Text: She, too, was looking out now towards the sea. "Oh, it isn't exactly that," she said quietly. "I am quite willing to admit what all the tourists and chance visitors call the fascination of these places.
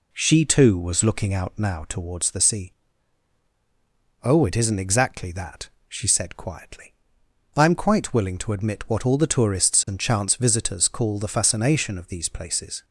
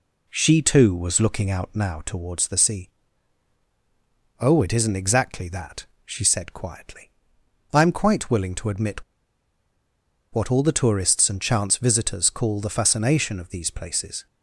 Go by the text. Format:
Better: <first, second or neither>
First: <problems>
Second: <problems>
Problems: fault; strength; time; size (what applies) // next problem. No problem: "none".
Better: first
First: none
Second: pauses between "admit" and "what"; strong; at 9.0 s; 1.3 s long